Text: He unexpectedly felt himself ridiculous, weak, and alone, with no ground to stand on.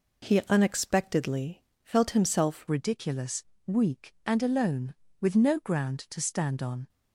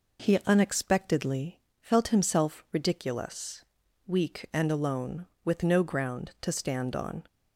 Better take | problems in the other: second | pauses between "unexpectedly" and "felt"; slight; at 1.6 s; 0.20 s long; slight in the second // changes voice at "ridiculous"; from 2.6 s on; 4.2 s long

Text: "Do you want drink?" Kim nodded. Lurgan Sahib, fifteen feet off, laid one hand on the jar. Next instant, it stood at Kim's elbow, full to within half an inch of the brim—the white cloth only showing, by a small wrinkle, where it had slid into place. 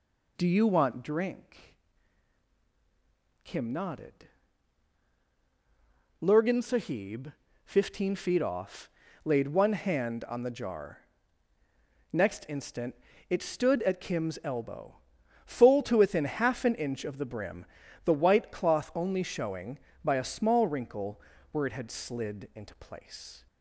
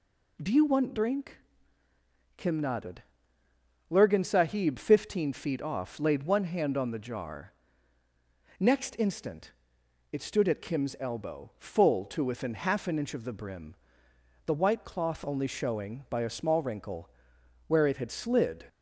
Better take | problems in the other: first | stops before "into place"; at 18.6 s

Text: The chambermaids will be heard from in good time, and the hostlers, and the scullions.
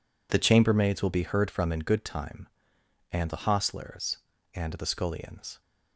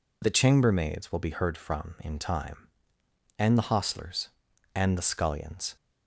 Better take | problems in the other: first | skips "good"; at 2.1 s

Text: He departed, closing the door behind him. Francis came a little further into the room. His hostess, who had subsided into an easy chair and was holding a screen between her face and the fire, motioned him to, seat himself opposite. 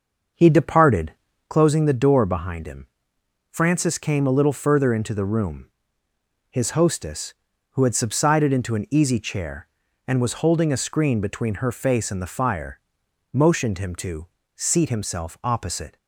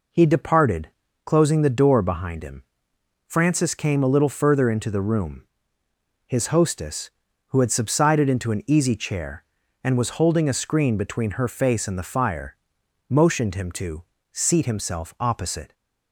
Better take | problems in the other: second | starts louder than the rest; until 1.7 s; 6.5 dB

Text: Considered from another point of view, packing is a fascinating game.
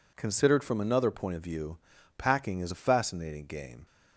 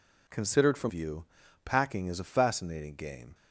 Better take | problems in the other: first | skips "another point of"; at 0.9 s

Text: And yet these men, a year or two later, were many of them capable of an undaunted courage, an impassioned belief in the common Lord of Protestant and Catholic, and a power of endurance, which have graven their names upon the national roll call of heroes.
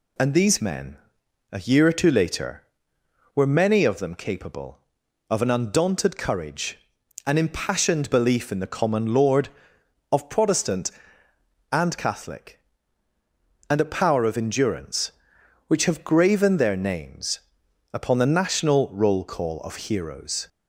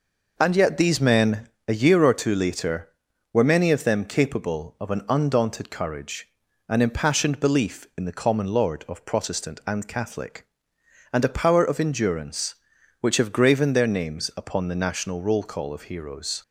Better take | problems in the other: second | skips "yet"; at 0.3 s // pauses between "names" and "upon"; noticeable; at 17.4 s; 0.52 s long

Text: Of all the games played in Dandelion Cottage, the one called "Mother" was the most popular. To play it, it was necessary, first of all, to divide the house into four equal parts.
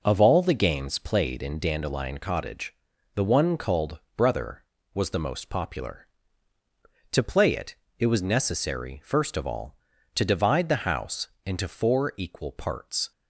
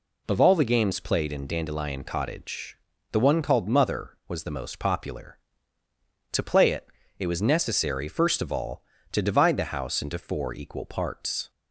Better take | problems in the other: second | says "Brother" for "Mother"; at 4.1 s // pauses between "house" and "into"; slight; at 11.2 s; 0.18 s long

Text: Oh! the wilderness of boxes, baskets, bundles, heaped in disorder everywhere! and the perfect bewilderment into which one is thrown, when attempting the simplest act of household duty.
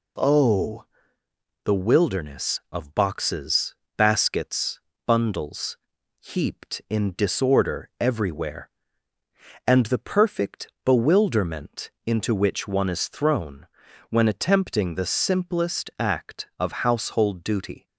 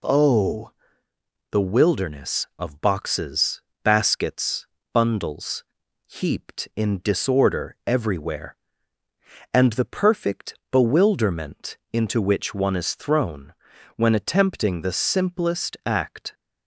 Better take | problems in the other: first | pauses between "perfect" and "bewilderment"; slight; at 10.5 s; 0.16 s long; slight in the first // stops before "of household duty"; at 16.3 s

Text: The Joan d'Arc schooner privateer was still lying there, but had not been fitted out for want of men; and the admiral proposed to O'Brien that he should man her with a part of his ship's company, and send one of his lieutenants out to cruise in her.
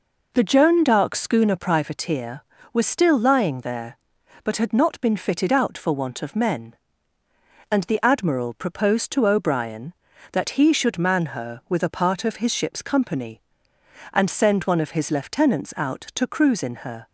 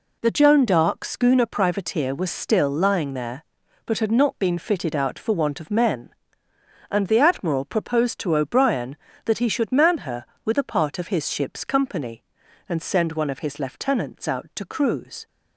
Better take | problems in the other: first | stops before "in her"; at 15.2 s

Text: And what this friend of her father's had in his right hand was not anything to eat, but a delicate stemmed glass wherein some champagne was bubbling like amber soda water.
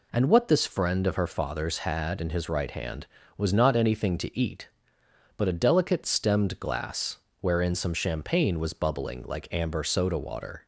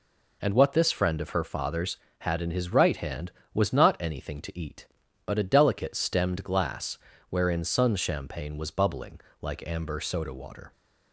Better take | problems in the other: first | pauses between "glass" and "wherein"; slight; at 6.9 s; 0.32 s long; slight in the first // says "sun" for "some"; at 7.6 s // pauses between "bubbling" and "like"; slight; at 9.1 s; 0.22 s long

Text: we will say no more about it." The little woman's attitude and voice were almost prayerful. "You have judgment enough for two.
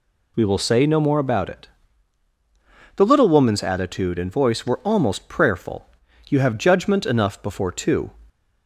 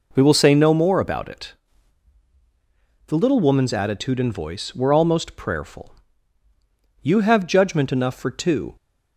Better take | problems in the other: second | says "before" for "for"; at 7.4 s

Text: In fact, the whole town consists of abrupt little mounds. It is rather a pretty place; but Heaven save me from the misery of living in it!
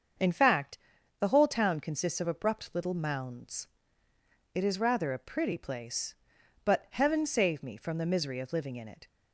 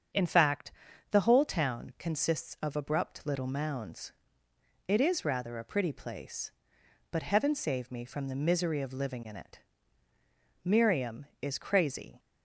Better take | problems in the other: first | starts louder than the rest; strong; until 1.5 s; 7 dB; also in the first // goes on to say "Miriam is crazy"; from 10.6 s on; 1.5 s long

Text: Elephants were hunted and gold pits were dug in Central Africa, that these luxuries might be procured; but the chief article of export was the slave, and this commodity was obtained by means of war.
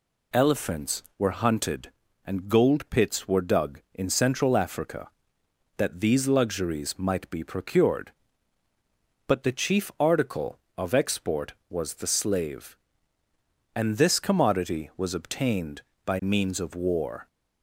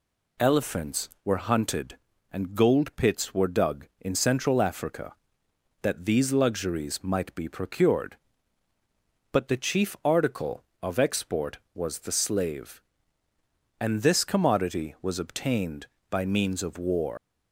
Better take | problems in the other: first | leaves "war" unfinished; at 17.1 s; 130 ms

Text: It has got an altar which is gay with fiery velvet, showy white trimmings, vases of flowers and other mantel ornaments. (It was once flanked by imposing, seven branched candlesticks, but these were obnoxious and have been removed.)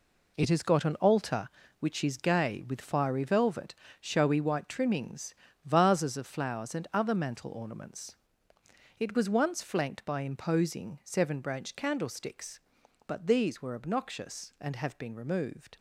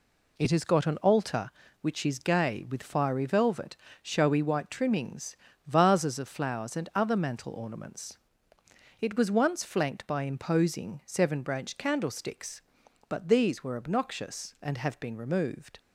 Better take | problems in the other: second | gets quieter; strong; throughout; 9 dB

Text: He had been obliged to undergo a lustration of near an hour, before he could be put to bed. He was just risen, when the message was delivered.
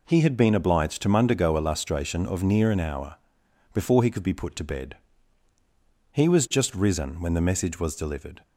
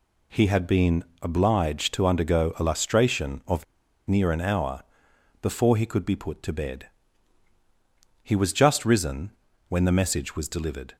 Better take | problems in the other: first | pauses between "been" and "obliged"; slight; at 1.0 s; 0.18 s long // pauses between "of" and "near"; at 3.6 s; 0.43 s long

